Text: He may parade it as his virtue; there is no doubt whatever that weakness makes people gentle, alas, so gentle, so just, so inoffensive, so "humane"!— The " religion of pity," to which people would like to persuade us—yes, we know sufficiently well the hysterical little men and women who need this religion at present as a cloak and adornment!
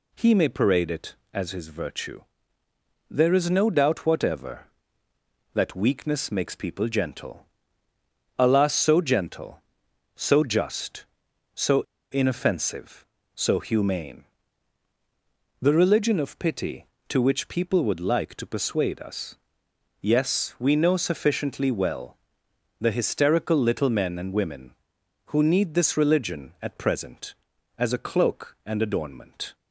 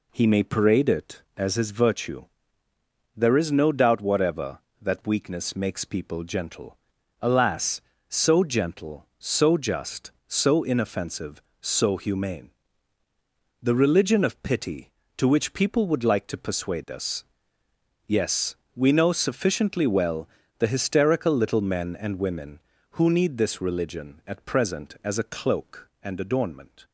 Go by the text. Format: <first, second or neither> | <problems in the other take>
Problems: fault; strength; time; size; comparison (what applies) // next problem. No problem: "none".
second | pauses between "so" and "inoffensive"; slight; at 11.8 s; 0.30 s long // pauses between "well" and "the"; noticeable; at 22.1 s; 0.62 s long; slight in the second